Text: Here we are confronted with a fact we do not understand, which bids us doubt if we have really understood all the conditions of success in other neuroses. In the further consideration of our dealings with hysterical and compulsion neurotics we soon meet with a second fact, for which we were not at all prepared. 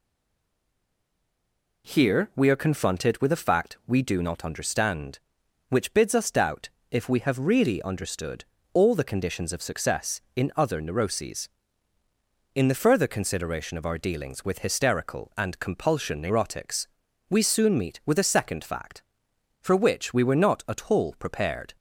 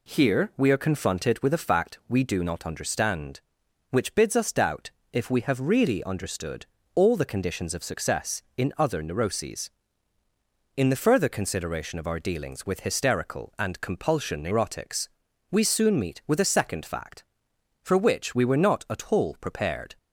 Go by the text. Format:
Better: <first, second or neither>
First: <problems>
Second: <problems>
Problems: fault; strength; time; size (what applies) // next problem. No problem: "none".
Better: second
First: stays silent before the first word; noticeable; until 1.8 s; 1.8 s long // pauses between "doubt" and "if"; slight; at 6.6 s; 0.20 s long // pauses between "understood" and "all"; slight; at 8.4 s; 0.30 s long // pauses between "neurotics" and "we"; at 16.8 s; 0.42 s long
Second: pauses between "doubt" and "if"; slight; at 4.9 s; 0.20 s long // pauses between "understood" and "all"; slight; at 6.6 s; 0.30 s long // pauses between "neurotics" and "we"; at 15.0 s; 0.42 s long